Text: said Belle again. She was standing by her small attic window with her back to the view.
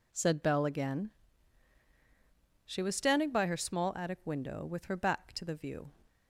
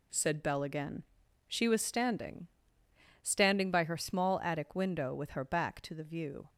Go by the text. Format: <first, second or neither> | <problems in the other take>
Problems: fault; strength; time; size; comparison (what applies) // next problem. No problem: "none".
first | says "standing" twice; at 3.2 s